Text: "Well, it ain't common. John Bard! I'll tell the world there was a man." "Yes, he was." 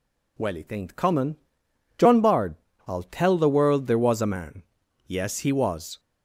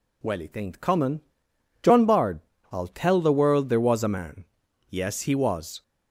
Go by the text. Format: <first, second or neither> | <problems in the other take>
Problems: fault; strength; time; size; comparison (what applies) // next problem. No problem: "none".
neither | none